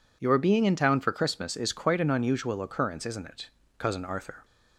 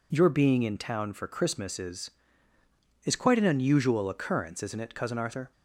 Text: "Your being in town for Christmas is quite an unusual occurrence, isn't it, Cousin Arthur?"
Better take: first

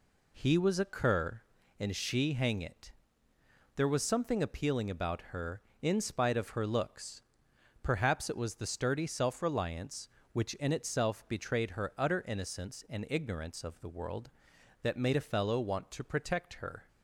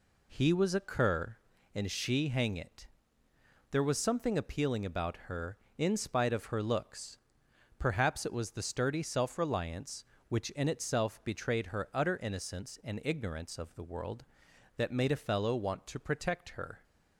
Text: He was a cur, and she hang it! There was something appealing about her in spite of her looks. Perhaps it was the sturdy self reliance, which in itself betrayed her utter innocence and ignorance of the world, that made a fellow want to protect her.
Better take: neither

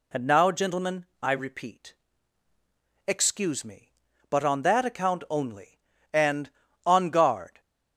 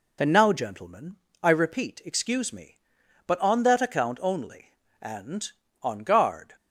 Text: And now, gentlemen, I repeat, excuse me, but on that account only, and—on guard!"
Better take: neither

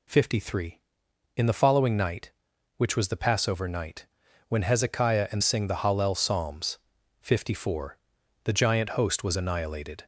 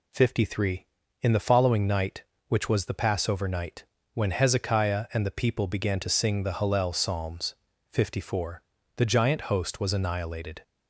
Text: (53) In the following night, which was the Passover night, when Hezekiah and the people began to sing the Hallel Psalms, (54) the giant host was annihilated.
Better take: second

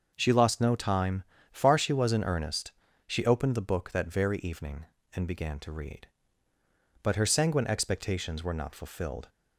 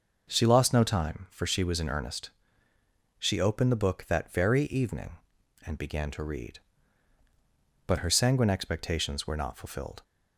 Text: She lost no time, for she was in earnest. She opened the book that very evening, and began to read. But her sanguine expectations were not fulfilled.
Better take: second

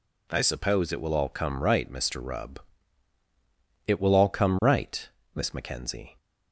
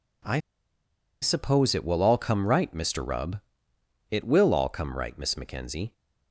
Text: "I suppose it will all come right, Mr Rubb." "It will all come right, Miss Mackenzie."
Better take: first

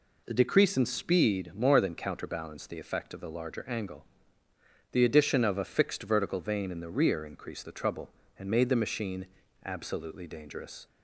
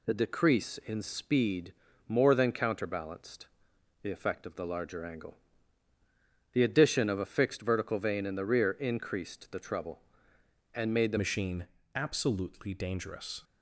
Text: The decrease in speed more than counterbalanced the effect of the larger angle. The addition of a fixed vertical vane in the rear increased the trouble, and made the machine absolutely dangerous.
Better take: first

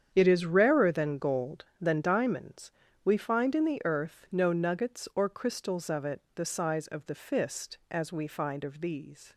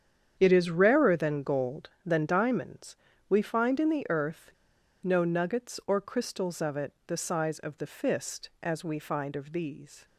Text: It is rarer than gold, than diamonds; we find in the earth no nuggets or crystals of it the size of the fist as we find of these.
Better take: first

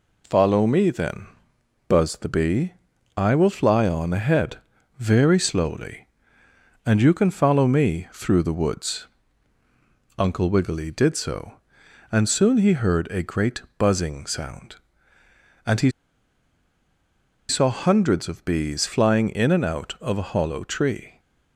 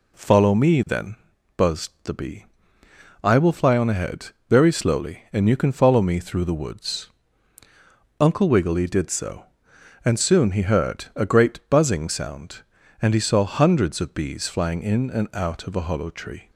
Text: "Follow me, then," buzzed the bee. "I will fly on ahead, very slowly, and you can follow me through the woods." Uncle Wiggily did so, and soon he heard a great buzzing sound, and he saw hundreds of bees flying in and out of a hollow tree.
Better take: second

